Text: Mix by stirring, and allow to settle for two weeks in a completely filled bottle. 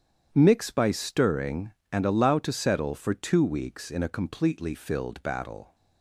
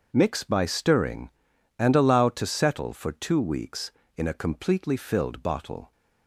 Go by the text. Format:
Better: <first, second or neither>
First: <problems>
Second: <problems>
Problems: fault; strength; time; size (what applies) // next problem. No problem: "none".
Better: second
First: starts louder than the rest; strong; until 1.3 s; 9 dB // says "battle" for "bottle"; at 5.2 s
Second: starts louder than the rest; until 1.1 s; 6.5 dB